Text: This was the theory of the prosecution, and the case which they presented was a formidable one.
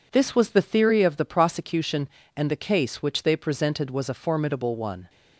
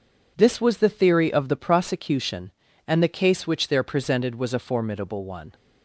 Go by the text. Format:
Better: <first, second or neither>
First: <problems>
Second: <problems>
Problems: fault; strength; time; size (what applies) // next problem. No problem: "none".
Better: first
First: none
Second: says "there" for "they"; at 3.6 s